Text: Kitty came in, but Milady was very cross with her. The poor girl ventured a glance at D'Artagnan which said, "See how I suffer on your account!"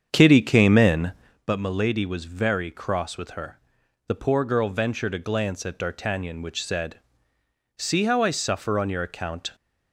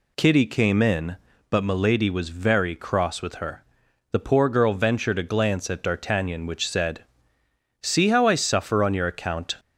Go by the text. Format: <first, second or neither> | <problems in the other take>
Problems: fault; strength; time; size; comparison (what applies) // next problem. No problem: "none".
second | starts louder than the rest; strong; until 1.4 s; 7.5 dB